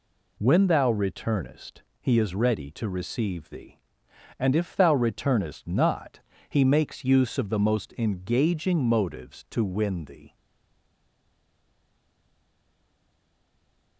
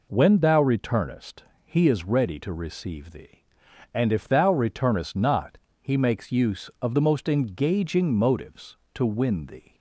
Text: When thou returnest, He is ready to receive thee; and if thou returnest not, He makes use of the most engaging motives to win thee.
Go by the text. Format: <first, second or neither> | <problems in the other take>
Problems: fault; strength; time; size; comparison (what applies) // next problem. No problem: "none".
second | stays silent after the last word; strong; from 10.3 s on; 3.6 s long